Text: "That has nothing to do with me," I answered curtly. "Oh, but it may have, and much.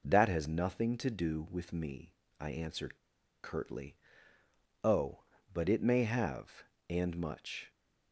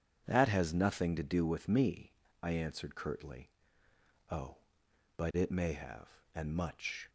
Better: second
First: pauses between "answered" and "curtly"; noticeable; at 2.9 s; 0.46 s long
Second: none

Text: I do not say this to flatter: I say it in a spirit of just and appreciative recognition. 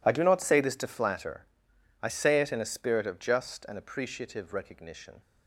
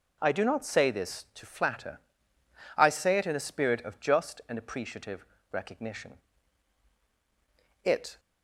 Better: first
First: none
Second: pauses between "appreciative" and "recognition"; slight; at 5.2 s; 0.26 s long // goes on to say "It"; slight; from 7.8 s on; 0.36 s long

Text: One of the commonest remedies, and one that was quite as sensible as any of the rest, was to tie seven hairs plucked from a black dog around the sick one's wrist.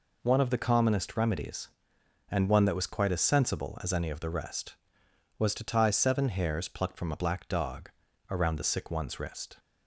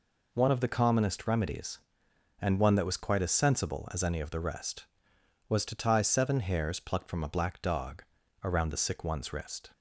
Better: neither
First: pauses between "dog" and "around"; slight; at 7.9 s; 0.36 s long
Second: pauses between "dog" and "around"; slight; at 8.0 s; 0.36 s long

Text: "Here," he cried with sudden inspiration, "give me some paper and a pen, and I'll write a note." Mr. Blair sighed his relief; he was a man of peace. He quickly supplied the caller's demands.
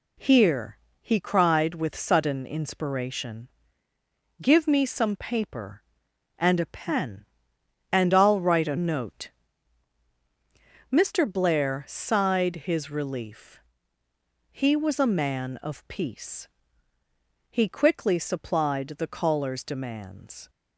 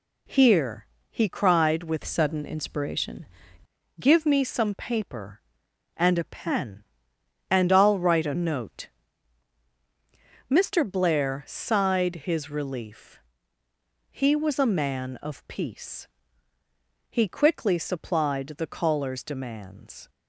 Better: first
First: none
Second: changes voice from "sudden" to "inspiration"; from 2.0 to 3.2 s; 1.2 s long

